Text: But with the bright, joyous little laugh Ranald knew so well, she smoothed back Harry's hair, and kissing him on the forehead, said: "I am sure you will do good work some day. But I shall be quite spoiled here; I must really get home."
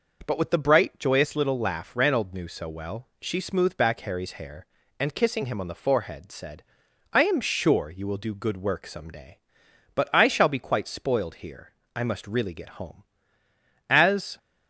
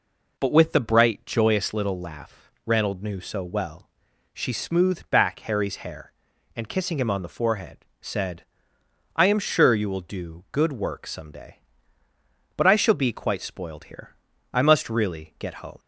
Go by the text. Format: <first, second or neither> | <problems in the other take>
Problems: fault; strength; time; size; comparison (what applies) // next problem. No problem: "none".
second | goes on to say "As"; slight; from 13.8 s on; 0.48 s long